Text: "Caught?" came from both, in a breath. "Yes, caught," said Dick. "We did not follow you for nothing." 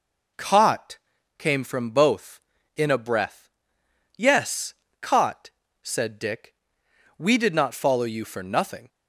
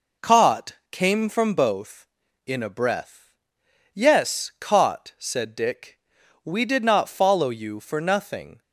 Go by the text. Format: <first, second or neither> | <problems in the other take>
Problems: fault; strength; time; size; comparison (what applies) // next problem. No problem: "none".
neither | none